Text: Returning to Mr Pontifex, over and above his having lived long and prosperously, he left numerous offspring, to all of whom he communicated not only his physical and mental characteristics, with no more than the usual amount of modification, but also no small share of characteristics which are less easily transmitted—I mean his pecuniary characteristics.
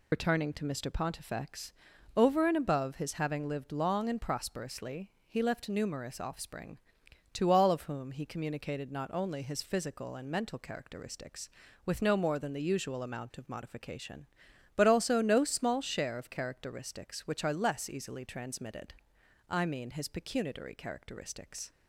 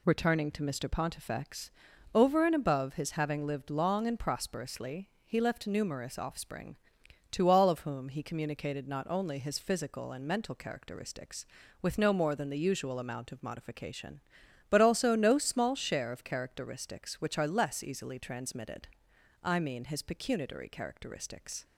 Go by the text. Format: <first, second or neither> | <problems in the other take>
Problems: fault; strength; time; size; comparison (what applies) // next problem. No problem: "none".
second | loses the start of "Returning"; at 0.1 s; 45 ms